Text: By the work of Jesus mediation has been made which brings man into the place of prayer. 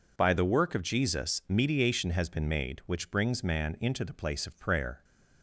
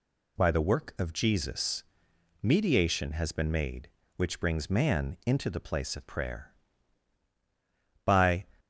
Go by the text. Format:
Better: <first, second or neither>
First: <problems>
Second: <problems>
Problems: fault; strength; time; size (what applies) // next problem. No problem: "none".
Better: first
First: none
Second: pauses between "Jesus" and "mediation"; noticeable; at 1.8 s; 0.60 s long // goes on to say "By"; slight; from 8.0 s on; 0.42 s long